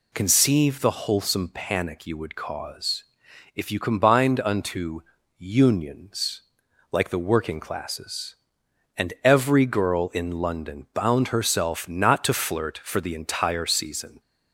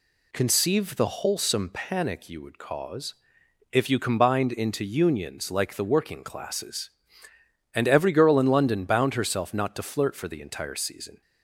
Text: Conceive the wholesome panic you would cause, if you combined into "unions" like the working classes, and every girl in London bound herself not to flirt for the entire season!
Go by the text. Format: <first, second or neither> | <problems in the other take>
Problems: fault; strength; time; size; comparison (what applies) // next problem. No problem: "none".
second | says "unto" for "into"; at 4.4 s // pauses between "unions" and "like"; noticeable; at 6.4 s; 0.48 s long